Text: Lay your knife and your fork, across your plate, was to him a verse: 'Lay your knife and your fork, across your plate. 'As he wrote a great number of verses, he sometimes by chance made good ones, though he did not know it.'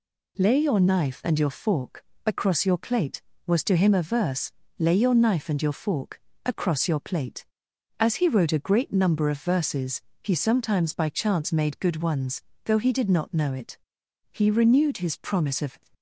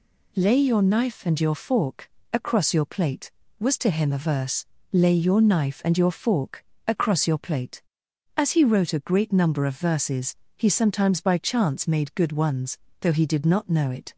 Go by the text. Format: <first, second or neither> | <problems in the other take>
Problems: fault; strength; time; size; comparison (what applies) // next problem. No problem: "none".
second | goes on to say "He renewed his promise of"; from 14.2 s on; 1.4 s long